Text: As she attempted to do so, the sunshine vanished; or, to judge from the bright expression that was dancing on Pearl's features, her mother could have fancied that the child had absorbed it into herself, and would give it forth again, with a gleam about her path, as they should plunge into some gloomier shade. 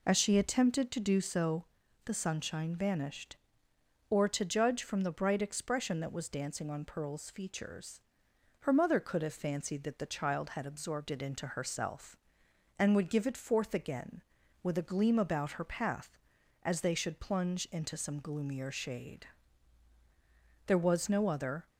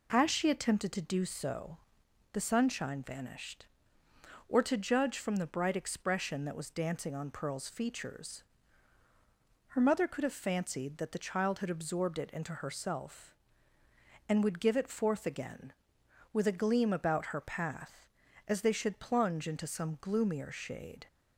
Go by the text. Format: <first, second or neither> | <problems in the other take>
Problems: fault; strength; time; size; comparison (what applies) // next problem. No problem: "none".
second | goes on to say "There was no other"; noticeable; from 20.6 s on; 1.0 s long